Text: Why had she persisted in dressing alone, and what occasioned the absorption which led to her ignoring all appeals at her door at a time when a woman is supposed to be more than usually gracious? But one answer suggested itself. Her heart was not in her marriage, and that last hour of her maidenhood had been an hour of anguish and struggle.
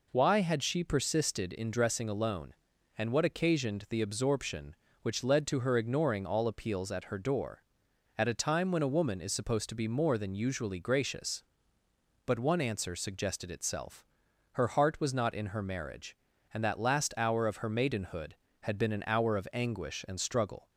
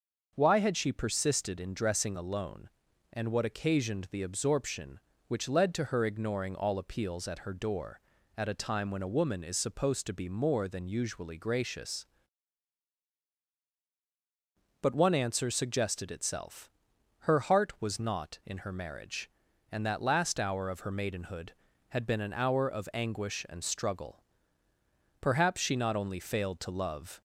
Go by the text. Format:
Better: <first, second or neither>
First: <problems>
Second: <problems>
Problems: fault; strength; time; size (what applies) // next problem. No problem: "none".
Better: first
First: none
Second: starts louder than the rest; noticeable; until 1.3 s; 6 dB // goes on to say "Perhaps she not only failed to love"; strong; from 25.2 s on; 2.0 s long